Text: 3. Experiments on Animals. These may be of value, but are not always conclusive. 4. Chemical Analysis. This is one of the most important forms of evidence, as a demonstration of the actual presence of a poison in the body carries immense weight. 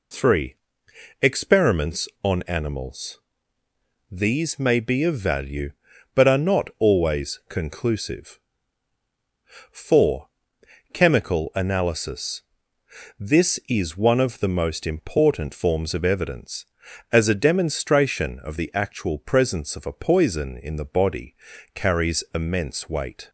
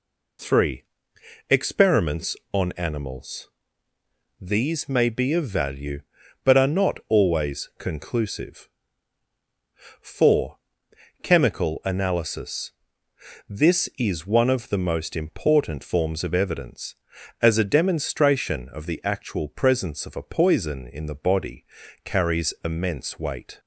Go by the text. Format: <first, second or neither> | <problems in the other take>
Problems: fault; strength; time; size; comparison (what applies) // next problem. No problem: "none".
neither | pauses between "body" and "carries"; the same in both